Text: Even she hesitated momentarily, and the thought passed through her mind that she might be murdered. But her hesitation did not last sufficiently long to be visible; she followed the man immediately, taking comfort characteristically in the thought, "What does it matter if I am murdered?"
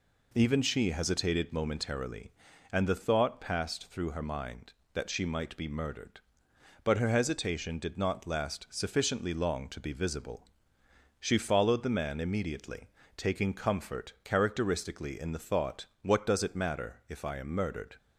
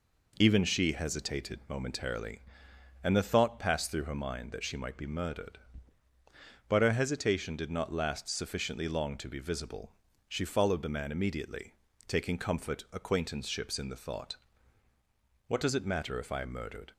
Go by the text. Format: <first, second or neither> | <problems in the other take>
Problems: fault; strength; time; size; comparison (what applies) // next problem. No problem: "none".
first | says "acquaintanceships" for "characteristically"; at 12.9 s